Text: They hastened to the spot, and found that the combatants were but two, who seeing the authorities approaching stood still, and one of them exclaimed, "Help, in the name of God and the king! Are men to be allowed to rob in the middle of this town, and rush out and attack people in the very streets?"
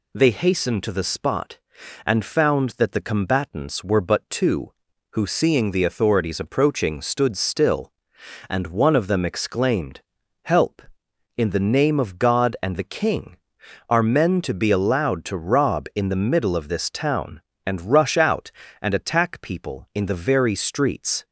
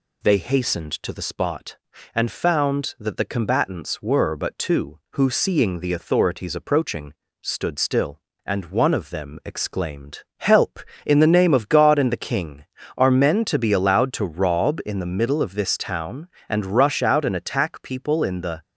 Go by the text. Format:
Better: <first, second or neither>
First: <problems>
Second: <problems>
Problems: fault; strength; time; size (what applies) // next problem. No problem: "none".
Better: first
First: none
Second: pauses between "approaching" and "stood"; slight; at 7.1 s; 0.28 s long // stops before "very streets"; at 18.6 s